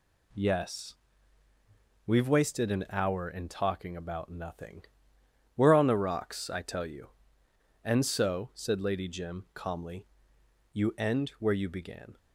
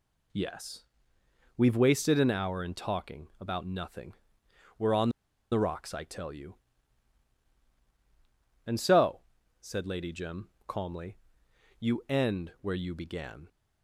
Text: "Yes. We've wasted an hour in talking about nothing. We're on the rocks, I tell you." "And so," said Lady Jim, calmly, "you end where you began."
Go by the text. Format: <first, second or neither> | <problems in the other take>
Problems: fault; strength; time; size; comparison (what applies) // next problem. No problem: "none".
first | pauses between "on" and "the"; at 5.0 s; 0.41 s long